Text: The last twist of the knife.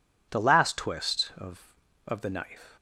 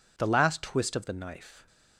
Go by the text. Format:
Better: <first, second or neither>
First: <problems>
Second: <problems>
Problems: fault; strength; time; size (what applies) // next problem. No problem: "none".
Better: second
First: says "of" twice; at 2.0 s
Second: none